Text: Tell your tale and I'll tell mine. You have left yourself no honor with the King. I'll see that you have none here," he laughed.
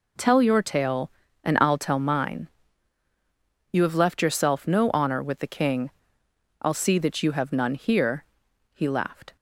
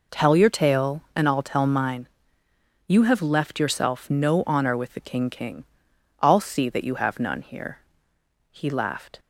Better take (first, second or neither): first